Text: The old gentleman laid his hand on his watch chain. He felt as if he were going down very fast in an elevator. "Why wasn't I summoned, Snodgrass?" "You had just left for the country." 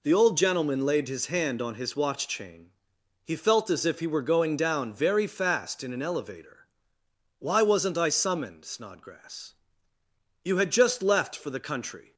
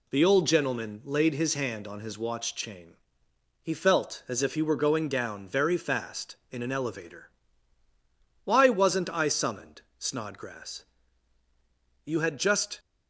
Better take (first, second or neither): first